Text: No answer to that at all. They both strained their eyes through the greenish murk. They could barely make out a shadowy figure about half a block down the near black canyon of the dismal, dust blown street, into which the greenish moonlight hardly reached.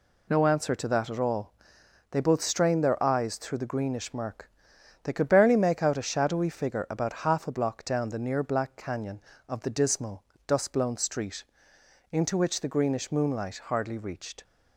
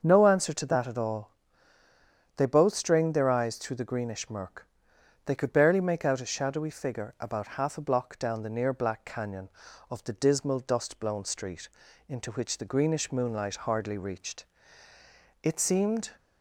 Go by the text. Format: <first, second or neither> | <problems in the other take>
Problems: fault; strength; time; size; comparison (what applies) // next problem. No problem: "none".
first | starts louder than the rest; until 1.0 s; 7 dB // goes on to say "It seemed"; noticeable; from 15.4 s on; 0.68 s long